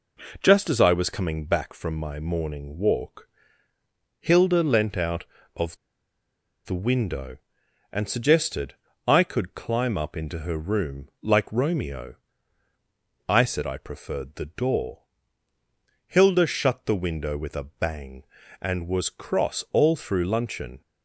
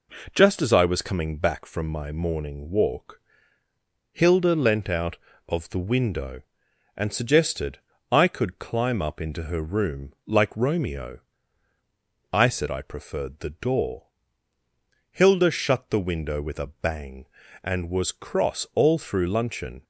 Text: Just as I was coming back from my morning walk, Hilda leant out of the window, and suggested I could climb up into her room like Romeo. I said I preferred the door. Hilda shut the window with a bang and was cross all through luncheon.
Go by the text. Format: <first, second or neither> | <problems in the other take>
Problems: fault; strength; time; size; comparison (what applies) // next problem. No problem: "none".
second | pauses between "of" and "the"; noticeable; at 5.7 s; 0.88 s long // pauses between "suggested" and "I"; slight; at 8.7 s; 0.32 s long; slight in the second